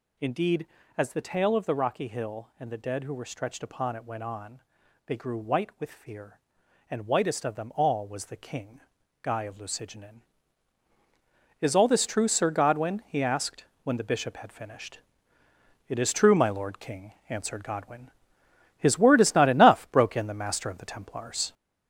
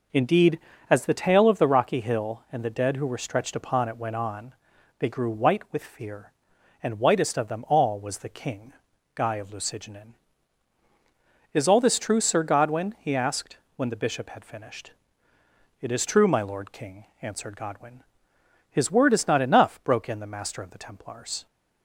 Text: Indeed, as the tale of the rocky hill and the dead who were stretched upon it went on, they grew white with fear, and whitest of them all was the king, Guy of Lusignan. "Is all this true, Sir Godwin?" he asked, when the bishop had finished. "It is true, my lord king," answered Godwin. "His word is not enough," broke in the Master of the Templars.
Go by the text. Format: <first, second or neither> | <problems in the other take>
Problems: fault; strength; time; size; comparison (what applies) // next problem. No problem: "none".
second | gets louder; noticeable; throughout; 4.5 dB